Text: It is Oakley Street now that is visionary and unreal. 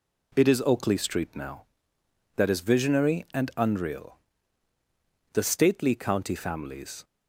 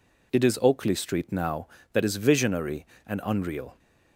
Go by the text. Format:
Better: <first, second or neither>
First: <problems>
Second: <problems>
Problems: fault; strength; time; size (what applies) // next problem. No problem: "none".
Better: second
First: goes on to say "The stately county families"; strong; from 5.3 s on; 1.7 s long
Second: none